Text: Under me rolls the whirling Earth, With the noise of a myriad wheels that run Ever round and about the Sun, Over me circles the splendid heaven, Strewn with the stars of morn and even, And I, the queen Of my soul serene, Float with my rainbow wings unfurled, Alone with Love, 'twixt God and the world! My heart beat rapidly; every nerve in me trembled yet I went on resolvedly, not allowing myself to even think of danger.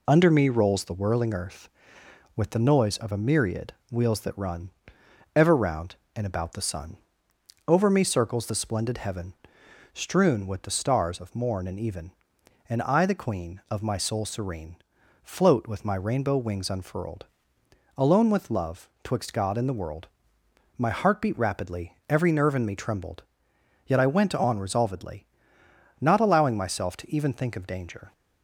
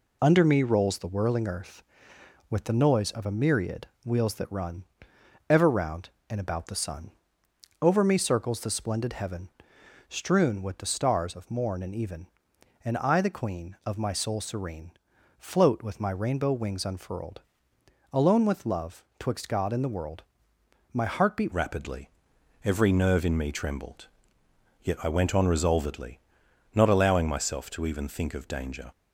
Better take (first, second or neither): first